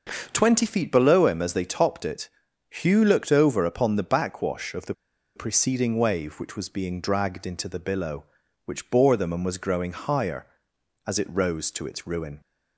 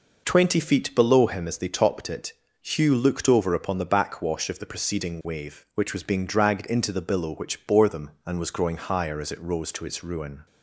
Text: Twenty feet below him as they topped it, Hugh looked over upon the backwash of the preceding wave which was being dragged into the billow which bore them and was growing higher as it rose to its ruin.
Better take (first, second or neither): second